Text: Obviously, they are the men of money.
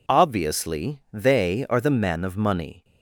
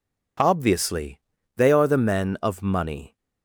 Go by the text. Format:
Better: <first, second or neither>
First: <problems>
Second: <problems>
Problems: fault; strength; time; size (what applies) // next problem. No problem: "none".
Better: neither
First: none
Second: none